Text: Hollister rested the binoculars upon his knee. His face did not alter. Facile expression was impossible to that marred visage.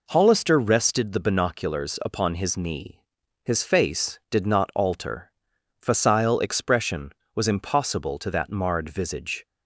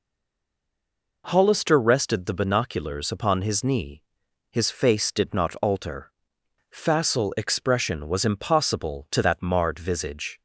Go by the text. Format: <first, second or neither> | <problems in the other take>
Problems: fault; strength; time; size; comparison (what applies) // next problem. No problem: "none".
first | stays silent before the first word; noticeable; until 1.2 s; 1.2 s long